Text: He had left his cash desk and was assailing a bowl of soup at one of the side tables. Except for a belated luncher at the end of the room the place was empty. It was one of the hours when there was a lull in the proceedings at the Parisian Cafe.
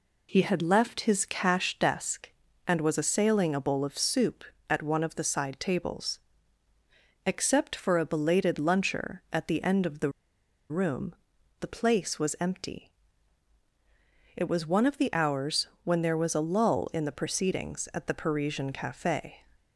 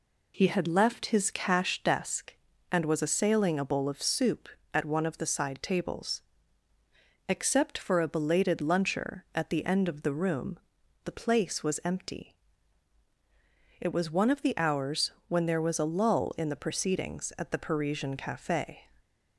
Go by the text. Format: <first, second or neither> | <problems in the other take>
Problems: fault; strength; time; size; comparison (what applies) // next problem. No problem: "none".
second | pauses between "the" and "room"; noticeable; at 10.0 s; 0.60 s long // pauses between "room" and "the"; noticeable; at 11.1 s; 0.46 s long; noticeable in the second // pauses between "hours" and "when"; slight; at 15.6 s; 0.18 s long; slight in the second